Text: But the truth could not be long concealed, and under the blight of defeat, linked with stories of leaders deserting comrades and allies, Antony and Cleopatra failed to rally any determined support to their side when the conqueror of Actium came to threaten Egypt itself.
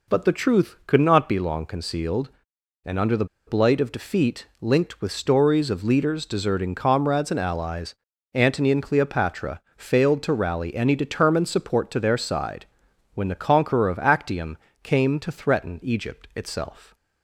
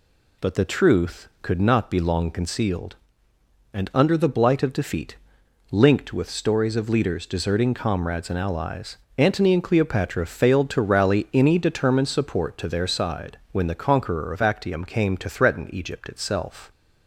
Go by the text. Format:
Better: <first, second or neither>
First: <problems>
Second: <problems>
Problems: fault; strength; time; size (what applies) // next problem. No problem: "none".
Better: second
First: pauses between "the" and "blight"; slight; at 3.2 s; 0.21 s long // pauses between "Cleopatra" and "failed"; slight; at 9.6 s; 0.16 s long // pauses between "side" and "when"; noticeable; at 12.6 s; 0.48 s long // pauses between "Actium" and "came"; slight; at 14.5 s; 0.24 s long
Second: none